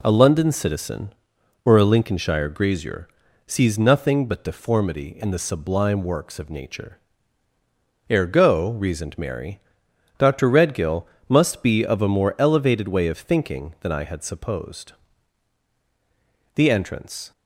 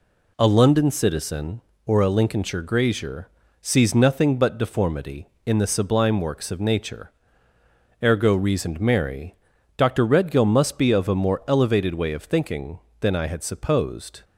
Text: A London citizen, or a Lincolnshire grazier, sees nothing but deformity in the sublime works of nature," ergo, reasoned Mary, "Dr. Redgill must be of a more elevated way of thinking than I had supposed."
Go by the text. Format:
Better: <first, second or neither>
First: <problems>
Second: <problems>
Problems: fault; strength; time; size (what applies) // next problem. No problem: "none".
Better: second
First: pauses between "Redgill" and "must"; slight; at 11.0 s; 0.24 s long // goes on to say "The entrance"; noticeable; from 16.5 s on; 0.76 s long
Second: none